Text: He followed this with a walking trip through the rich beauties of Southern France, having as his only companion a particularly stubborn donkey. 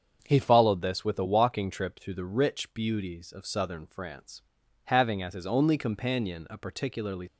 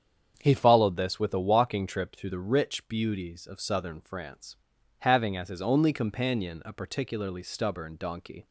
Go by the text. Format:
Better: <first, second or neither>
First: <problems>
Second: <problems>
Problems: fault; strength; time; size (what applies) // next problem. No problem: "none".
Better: second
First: starts louder than the rest; until 1.2 s; 7 dB // stops before "stubborn donkey"; at 7.2 s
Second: starts louder than the rest; strong; until 1.4 s; 8 dB